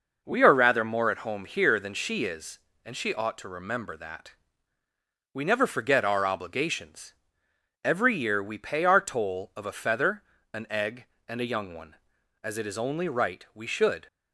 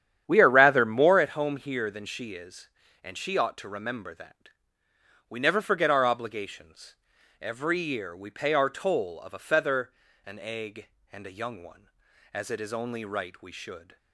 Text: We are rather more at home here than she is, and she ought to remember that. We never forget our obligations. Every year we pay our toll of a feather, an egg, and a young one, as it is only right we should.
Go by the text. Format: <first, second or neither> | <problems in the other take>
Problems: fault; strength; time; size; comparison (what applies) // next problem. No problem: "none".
first | starts louder than the rest; strong; until 1.2 s; 9.5 dB